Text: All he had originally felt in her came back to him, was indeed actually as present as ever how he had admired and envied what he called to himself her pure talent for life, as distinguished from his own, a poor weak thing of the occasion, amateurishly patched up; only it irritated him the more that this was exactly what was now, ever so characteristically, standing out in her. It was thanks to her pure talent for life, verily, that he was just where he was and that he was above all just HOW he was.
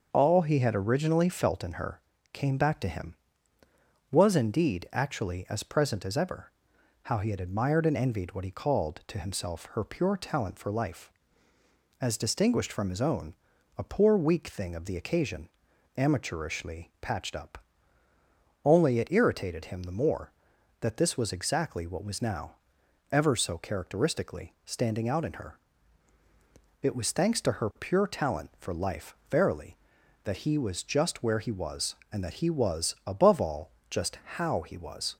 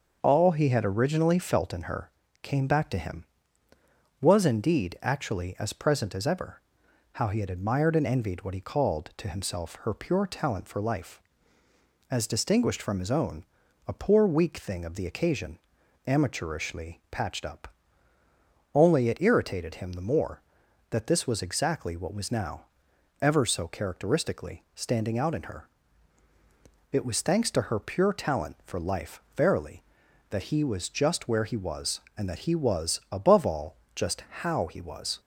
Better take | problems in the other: neither | starts louder than the rest; the same in both // pauses between "her" and "came"; slight; the same in both // pauses between "ever" and "how"; noticeable; the same in both // pauses between "all" and "just"; slight; the same in both

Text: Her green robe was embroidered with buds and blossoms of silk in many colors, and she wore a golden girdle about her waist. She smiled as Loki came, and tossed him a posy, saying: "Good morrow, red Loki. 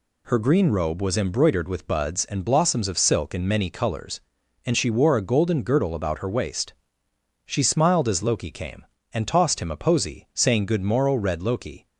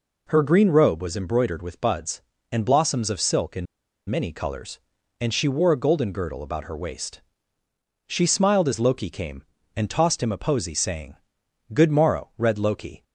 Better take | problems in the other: first | pauses between "in" and "many"; at 3.6 s; 0.43 s long

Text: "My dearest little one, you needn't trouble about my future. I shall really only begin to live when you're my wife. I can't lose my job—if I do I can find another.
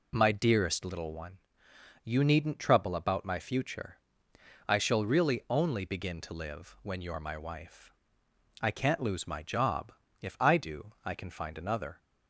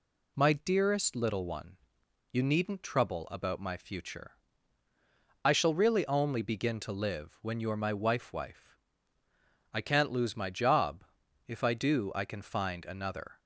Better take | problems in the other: first | says "wife" twice; at 8.3 s

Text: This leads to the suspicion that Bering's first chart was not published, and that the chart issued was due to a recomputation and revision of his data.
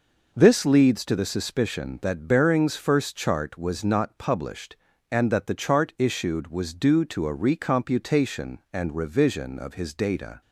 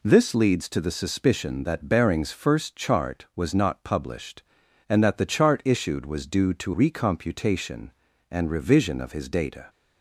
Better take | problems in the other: first | skips "a"; at 6.7 s

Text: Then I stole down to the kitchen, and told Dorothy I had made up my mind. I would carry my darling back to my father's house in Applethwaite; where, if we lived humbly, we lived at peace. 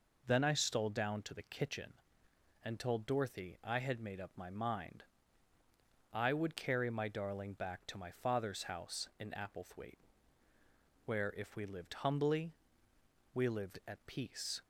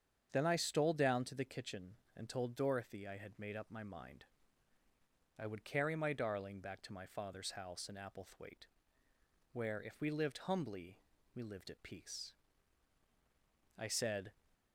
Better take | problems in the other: first | starts louder than the rest; strong; until 1.3 s; 7.5 dB // goes on to say "I said"; from 13.7 s on; 0.54 s long

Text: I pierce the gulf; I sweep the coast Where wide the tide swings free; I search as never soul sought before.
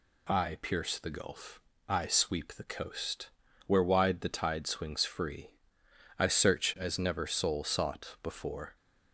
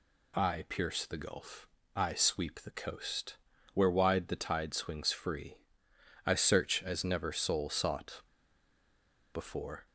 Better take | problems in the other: first | pauses between "coast" and "Where"; slight; at 3.3 s; 0.36 s long; slight in the first // pauses between "sought" and "before"; at 8.2 s; 1.1 s long

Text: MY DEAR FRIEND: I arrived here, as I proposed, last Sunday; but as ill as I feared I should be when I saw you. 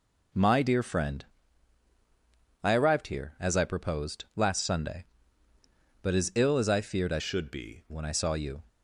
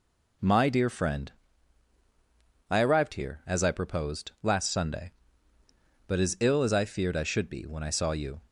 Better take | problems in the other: second | changes voice from "should" to "be"; from 7.1 to 7.8 s; 0.7 s long

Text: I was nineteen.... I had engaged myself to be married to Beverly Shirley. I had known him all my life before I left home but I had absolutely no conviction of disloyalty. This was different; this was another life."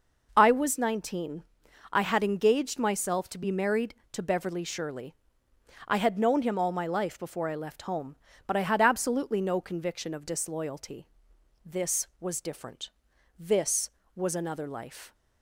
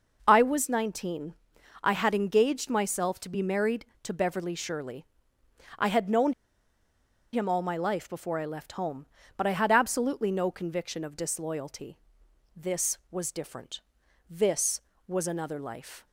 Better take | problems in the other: first | pauses between "known" and "him"; at 6.3 s; 1.0 s long

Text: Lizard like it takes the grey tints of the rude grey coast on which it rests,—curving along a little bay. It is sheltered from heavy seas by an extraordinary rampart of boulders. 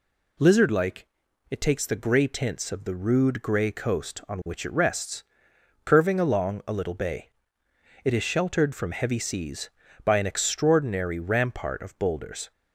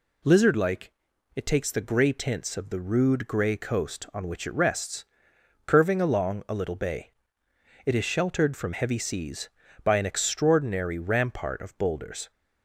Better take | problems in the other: neither | pauses between "like" and "it"; noticeable; the same in both

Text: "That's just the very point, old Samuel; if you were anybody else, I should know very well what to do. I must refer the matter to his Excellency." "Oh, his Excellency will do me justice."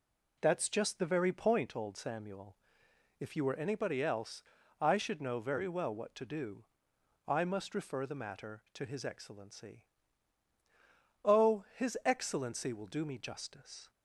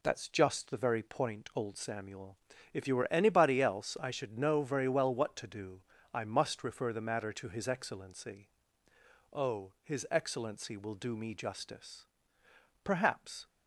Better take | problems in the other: first | goes on to say "Perhaps"; noticeable; from 12.8 s on; 0.62 s long

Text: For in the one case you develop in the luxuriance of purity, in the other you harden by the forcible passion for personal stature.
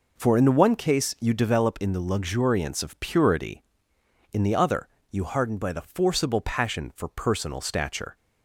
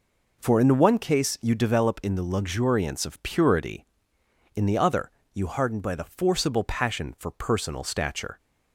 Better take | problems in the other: neither | pauses between "other" and "you"; slight; the same in both

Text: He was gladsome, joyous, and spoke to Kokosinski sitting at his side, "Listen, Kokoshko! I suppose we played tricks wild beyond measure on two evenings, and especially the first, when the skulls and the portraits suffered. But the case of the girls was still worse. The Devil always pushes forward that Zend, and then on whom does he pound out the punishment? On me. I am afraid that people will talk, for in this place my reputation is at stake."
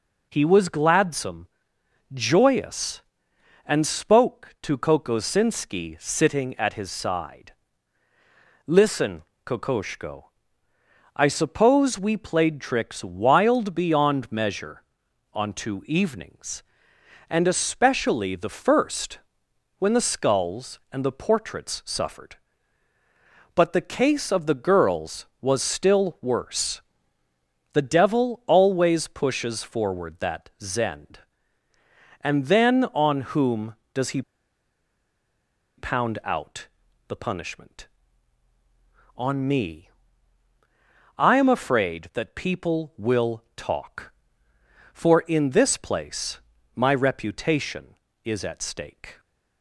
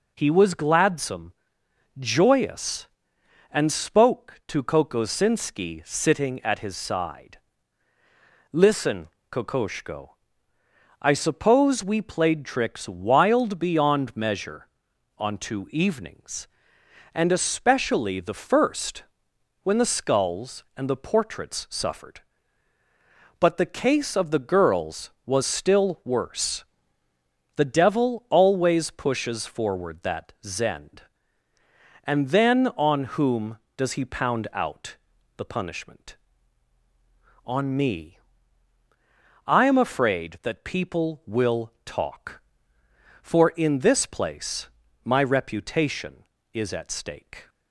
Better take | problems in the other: second | pauses between "he" and "pound"; strong; at 34.2 s; 1.5 s long // pauses between "out" and "the"; at 36.6 s; 0.40 s long; also in the second // pauses between "place" and "my"; slight; at 46.3 s; 0.36 s long; slight in the second

